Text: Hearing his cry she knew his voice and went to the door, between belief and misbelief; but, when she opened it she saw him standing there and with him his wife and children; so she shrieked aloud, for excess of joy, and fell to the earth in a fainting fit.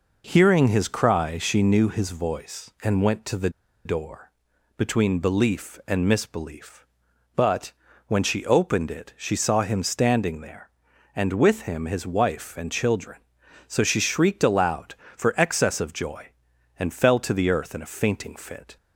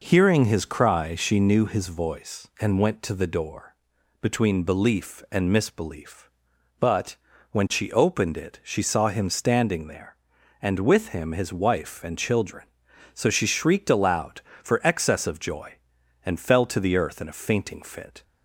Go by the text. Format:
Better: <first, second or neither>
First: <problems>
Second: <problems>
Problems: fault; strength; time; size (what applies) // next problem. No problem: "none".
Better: second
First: pauses between "the" and "door"; slight; at 3.4 s; 0.35 s long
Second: none